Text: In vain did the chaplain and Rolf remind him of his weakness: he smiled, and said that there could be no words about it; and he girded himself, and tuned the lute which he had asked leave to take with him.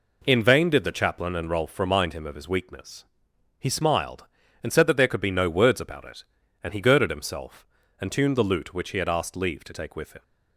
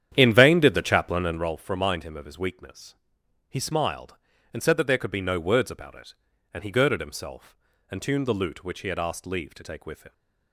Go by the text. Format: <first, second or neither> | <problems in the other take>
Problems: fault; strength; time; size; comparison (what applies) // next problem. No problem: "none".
first | starts louder than the rest; strong; until 1.5 s; 9.5 dB